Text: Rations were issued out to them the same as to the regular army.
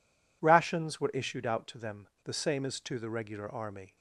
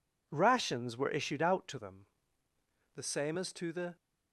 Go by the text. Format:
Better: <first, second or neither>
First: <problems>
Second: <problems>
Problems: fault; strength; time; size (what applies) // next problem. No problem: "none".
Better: first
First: pauses between "them" and "the"; slight; at 2.0 s; 0.16 s long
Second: pauses between "them" and "the"; noticeable; at 2.0 s; 0.90 s long // stops before "regular army"; at 3.9 s